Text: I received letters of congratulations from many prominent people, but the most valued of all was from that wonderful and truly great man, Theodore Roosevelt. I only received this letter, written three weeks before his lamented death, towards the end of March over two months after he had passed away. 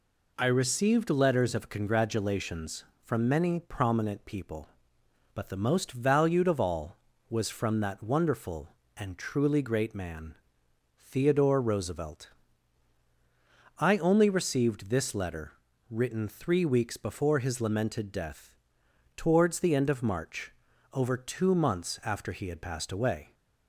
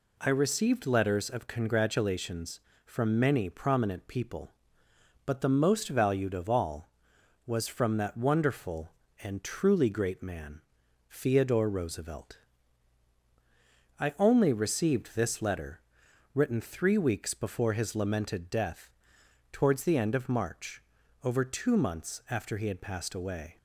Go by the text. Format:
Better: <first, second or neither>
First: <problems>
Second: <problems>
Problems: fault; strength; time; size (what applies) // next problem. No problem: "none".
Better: neither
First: pauses between "March" and "over"; at 20.5 s; 0.42 s long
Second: pauses between "March" and "over"; at 20.8 s; 0.42 s long